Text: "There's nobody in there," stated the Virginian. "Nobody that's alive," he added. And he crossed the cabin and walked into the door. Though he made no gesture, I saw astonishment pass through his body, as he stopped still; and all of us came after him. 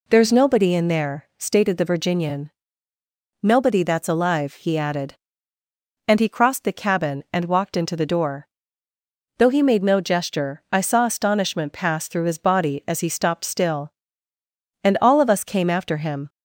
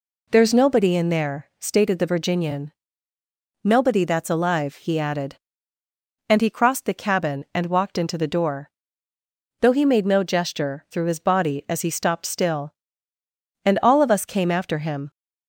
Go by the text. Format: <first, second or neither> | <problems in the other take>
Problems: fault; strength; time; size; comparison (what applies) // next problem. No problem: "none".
first | skips "I saw astonishment pass"; at 10.8 s